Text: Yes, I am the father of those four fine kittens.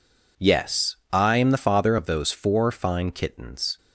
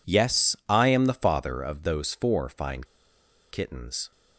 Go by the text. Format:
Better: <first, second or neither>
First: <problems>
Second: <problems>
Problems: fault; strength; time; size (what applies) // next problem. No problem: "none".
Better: first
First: none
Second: pauses between "fine" and "kittens"; noticeable; at 2.8 s; 0.66 s long